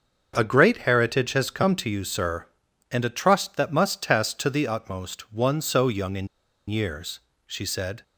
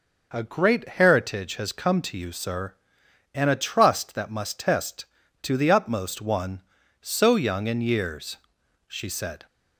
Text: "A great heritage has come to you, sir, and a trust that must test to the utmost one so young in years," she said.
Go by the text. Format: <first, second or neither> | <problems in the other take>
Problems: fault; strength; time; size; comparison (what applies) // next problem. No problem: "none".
second | starts louder than the rest; until 1.3 s; 6.5 dB // pauses between "in" and "years"; at 6.2 s; 0.40 s long